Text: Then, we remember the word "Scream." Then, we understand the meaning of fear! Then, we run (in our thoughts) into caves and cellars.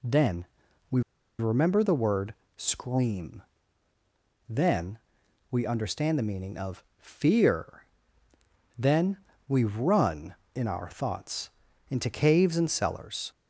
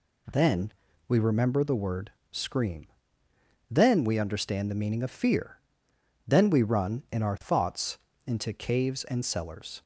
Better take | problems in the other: second | pauses between "we" and "remember"; at 1.0 s; 0.38 s long // pauses between "word" and "Scream"; slight; at 2.3 s; 0.22 s long; slight in the second // pauses between "of" and "fear"; slight; at 6.8 s; 0.16 s long

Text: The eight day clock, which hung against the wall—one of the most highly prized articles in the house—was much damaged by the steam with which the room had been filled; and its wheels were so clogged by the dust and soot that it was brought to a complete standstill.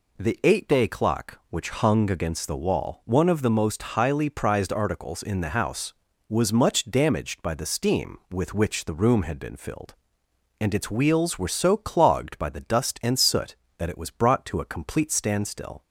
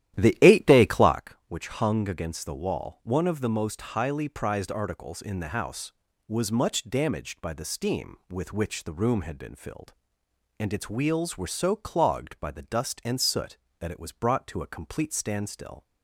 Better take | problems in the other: first | starts louder than the rest; strong; until 1.2 s; 12.5 dB

